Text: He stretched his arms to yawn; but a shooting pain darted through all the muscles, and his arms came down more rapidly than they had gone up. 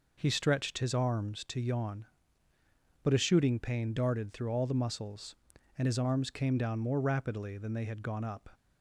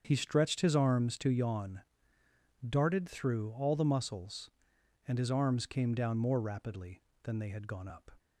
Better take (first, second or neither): first